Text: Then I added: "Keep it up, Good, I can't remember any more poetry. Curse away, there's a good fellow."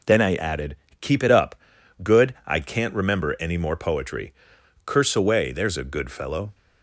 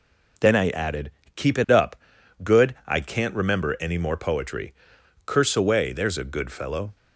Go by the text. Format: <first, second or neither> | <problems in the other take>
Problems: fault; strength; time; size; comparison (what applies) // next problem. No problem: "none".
neither | none